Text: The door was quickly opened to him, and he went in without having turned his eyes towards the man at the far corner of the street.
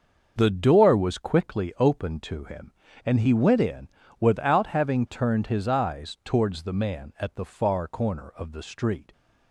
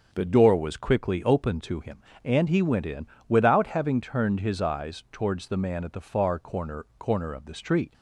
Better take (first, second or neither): first